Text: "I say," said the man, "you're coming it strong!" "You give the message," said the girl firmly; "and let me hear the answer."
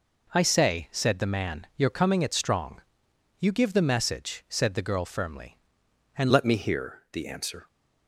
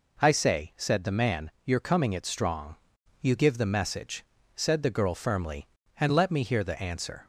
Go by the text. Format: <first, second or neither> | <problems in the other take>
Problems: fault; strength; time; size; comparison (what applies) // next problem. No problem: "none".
second | changes voice at "let"; from 6.2 s on; 1.4 s long